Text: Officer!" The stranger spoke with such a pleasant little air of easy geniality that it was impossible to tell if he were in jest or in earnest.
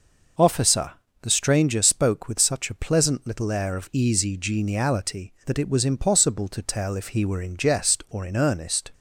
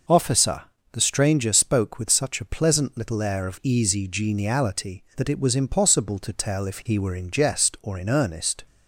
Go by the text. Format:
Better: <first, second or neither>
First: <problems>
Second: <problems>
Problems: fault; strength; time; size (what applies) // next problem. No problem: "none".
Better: neither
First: none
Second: none